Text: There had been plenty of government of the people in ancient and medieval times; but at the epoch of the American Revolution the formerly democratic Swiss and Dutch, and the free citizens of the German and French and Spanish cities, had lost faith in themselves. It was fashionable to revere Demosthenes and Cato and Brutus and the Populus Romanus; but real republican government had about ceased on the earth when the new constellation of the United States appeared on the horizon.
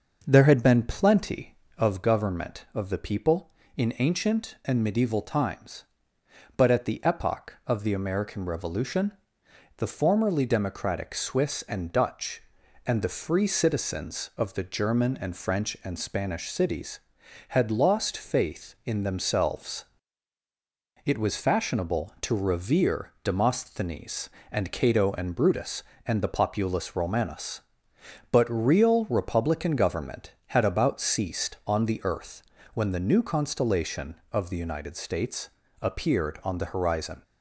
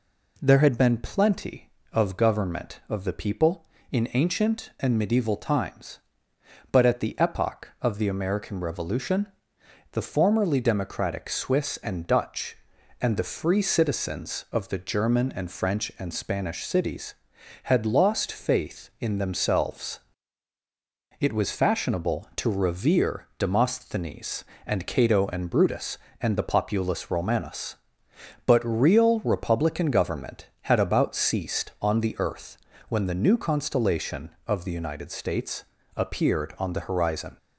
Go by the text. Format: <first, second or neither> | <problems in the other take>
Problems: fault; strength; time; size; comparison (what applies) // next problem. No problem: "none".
second | starts louder than the rest; until 1.9 s; 6 dB // pauses between "Revolution" and "the"; noticeable; at 9.1 s; 0.66 s long; noticeable in the second // pauses between "earth" and "when"; slight; at 32.4 s; 0.32 s long; slight in the second // pauses between "States" and "appeared"; slight; at 35.5 s; 0.30 s long; slight in the second